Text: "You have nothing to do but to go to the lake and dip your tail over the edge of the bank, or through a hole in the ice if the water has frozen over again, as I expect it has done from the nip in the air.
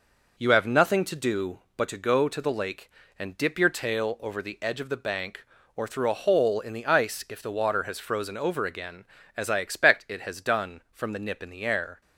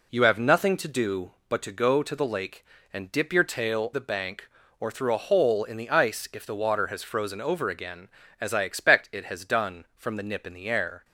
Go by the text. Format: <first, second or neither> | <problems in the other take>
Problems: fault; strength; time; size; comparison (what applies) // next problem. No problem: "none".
first | skips "over the edge of"; at 3.9 s